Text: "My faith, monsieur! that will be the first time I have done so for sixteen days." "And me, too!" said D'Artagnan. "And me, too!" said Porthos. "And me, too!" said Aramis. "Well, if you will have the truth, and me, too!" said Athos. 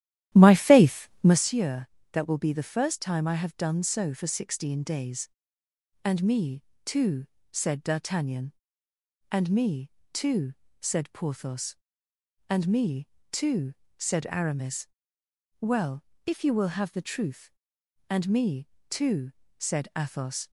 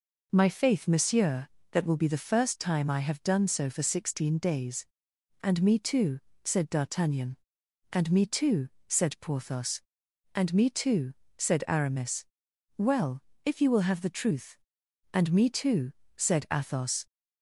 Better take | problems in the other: second | starts louder than the rest; strong; until 1.4 s; 12.5 dB

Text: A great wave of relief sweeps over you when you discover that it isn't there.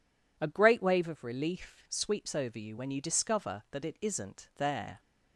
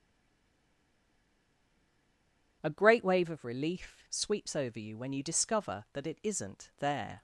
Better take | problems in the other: first | stays silent before the first word; strong; until 2.6 s; 2.6 s long

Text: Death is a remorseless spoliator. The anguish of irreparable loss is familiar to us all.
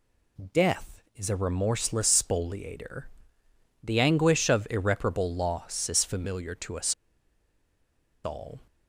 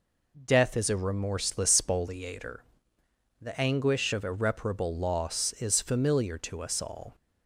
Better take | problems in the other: second | pauses between "us" and "all"; strong; at 6.9 s; 1.3 s long

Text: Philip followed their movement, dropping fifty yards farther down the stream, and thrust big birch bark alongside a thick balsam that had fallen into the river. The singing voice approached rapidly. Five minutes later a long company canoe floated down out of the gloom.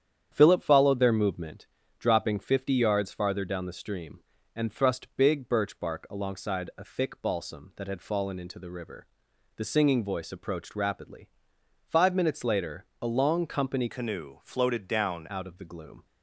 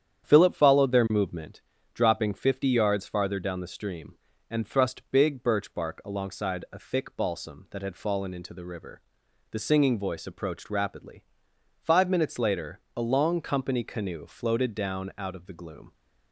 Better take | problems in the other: second | starts louder than the rest; strong; until 1.3 s; 9.5 dB; strong in the second // changes voice from "canoe" to "down"; from 13.8 to 15.2 s; 1.4 s long

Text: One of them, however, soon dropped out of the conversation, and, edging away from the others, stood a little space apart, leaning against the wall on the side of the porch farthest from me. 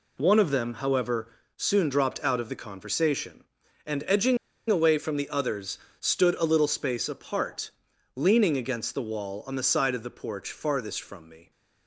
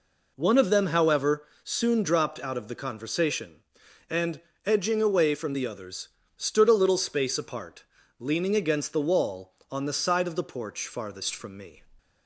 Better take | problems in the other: second | pauses between "edging" and "away"; slight; at 4.3 s; 0.33 s long

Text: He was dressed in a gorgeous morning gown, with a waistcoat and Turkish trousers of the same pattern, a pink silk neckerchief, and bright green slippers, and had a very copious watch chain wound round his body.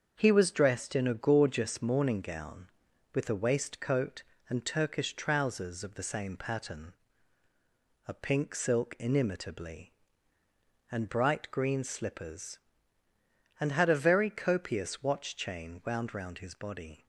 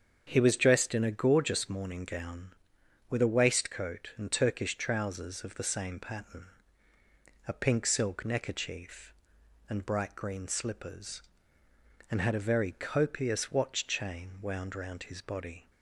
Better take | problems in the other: second | starts louder than the rest; until 1.1 s; 7 dB; strong in the second // says "inimitably" for "neckerchief"; at 8.9 s

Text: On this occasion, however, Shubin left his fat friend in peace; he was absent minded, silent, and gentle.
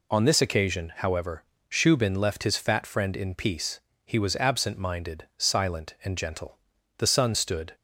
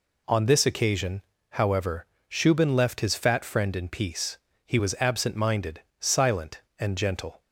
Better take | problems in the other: second | goes on to say "The sun stood"; noticeable; from 6.9 s on; 0.77 s long

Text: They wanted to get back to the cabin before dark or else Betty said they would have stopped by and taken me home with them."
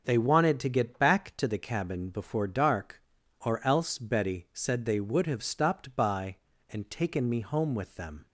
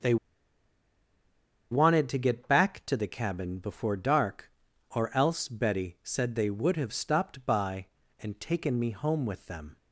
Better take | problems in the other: first | starts louder than the rest; until 2.5 s; 6.5 dB // pauses between "They" and "wanted"; strong; at 0.1 s; 1.5 s long

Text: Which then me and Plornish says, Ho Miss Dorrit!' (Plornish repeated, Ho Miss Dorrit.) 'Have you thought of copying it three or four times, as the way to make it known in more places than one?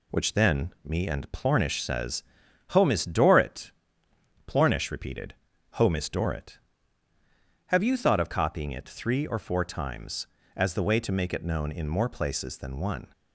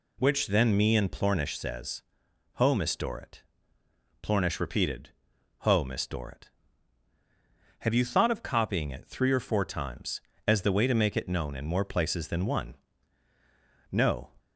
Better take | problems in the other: first | goes on to say "No"; slight; from 13.9 s on; 0.40 s long

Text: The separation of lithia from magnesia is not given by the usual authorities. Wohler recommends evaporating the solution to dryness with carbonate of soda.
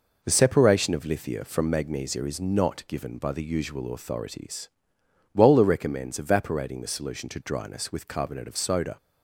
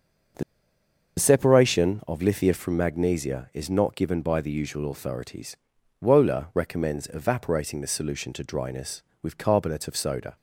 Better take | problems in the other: first | starts louder than the rest; until 2.1 s; 6.5 dB // pauses between "The" and "separation"; noticeable; at 0.4 s; 0.76 s long

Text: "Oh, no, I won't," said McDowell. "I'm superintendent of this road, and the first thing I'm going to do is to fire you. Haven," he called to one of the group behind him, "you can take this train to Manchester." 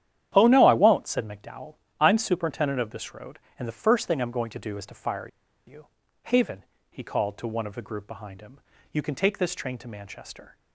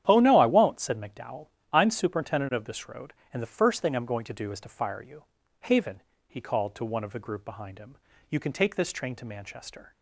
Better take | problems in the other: second | starts louder than the rest; strong; until 1.3 s; 10.5 dB; strong in the second // pauses between "fire" and "you"; at 5.2 s; 0.39 s long

